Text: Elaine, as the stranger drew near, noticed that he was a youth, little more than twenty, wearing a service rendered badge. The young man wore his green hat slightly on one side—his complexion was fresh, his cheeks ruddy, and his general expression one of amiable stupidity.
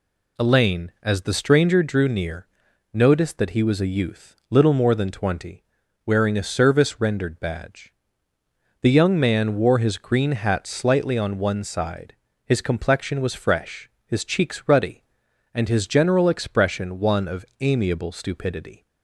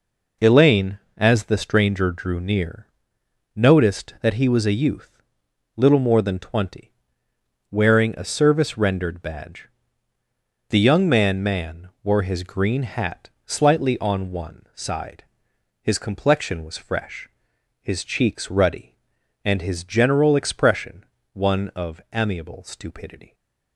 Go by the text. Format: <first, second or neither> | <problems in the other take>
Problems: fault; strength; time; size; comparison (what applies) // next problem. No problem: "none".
first | says "man" twice; at 11.4 s // pauses between "hat" and "slightly"; slight; at 13.3 s; 0.16 s long // pauses between "expression" and "one"; slight; at 21.0 s; 0.28 s long